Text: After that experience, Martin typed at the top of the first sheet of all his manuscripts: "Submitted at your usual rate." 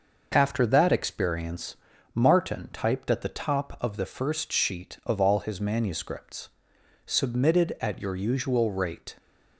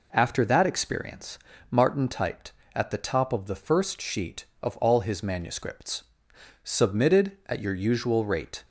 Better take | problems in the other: neither | none

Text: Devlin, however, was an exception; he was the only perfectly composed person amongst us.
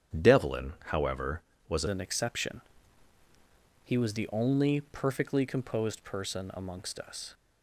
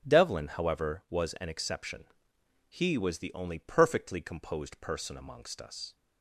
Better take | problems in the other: second | starts louder than the rest; strong; until 1.3 s; 9 dB; strong in the second // changes voice at "an"; from 1.8 s on; 5.5 s long

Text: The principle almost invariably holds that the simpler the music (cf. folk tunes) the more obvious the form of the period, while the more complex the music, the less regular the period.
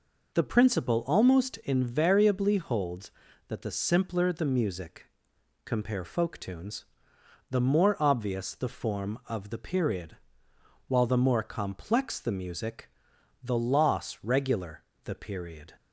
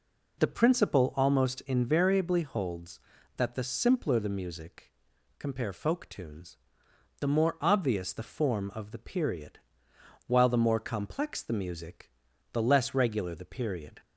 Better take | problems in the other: second | says "loss" for "less"; at 13.5 s // pauses between "regular" and "the"; slight; at 14.8 s; 0.18 s long

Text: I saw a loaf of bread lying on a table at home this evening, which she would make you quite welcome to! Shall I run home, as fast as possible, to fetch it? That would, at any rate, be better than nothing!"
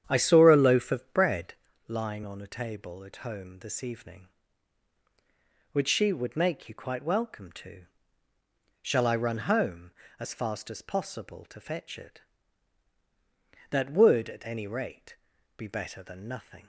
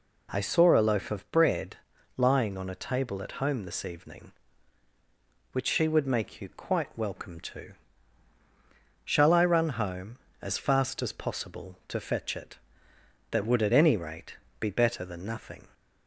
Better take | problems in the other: second | starts louder than the rest; strong; until 1.7 s; 9 dB // pauses between "bread" and "lying"; slight; at 1.5 s; 0.34 s long; also in the second

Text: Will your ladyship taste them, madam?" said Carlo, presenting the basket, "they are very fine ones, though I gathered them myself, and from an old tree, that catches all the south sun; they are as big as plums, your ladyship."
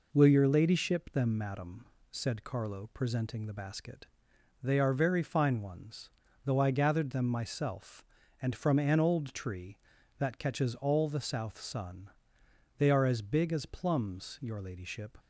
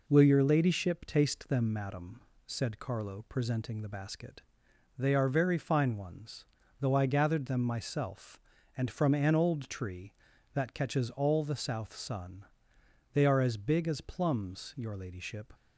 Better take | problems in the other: second | skips "taste"; at 1.1 s

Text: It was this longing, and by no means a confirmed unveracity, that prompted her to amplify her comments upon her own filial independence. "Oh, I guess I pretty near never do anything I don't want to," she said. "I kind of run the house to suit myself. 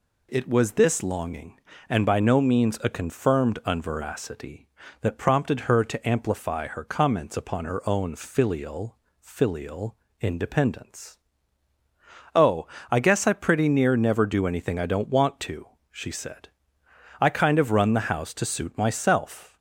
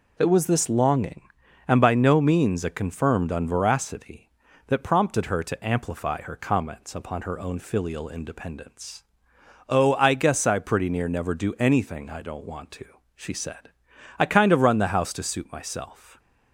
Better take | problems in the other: second | says "filial" twice; at 9.1 s

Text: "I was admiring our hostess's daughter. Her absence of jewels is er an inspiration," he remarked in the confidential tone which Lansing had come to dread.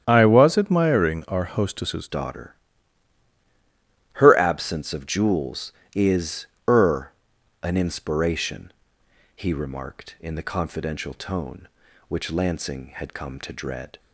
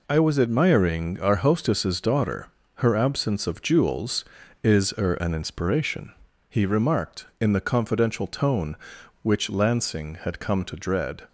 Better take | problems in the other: second | starts louder than the rest; strong; until 1.0 s; 9.5 dB // changes voice at "daughter"; from 2.0 s on; 11.9 s long // pauses between "is" and "er"; slight; at 6.4 s; 0.20 s long // pauses between "er" and "an"; noticeable; at 7.1 s; 0.50 s long

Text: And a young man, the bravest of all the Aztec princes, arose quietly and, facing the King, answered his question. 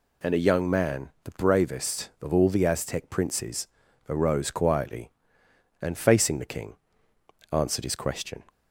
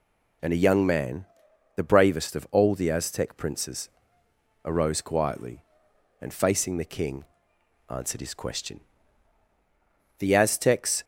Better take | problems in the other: first | goes on to say "The Aztecs"; noticeable; from 10.1 s on; 0.84 s long

